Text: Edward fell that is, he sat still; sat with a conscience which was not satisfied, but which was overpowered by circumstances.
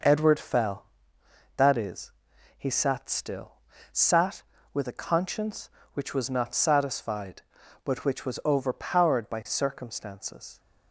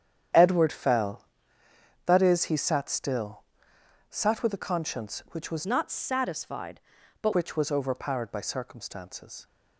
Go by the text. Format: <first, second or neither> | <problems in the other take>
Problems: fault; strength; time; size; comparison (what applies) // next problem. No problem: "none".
first | starts louder than the rest; strong; until 2.1 s; 9 dB // changes voice from "not" to "but"; from 5.6 to 7.3 s; 1.7 s long